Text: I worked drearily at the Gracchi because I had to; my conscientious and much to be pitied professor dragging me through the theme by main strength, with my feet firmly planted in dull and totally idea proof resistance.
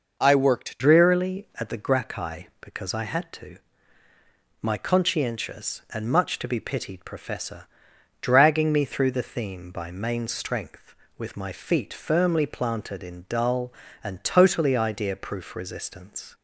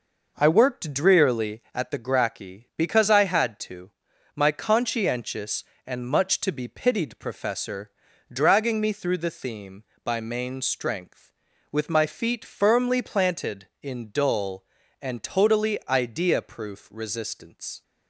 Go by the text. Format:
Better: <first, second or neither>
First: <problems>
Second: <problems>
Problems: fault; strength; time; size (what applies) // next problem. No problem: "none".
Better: second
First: changes voice at "drearily"; from 0.7 s on; 15.6 s long // pauses between "professor" and "dragging"; noticeable; at 7.6 s; 0.58 s long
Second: pauses between "professor" and "dragging"; at 7.9 s; 0.40 s long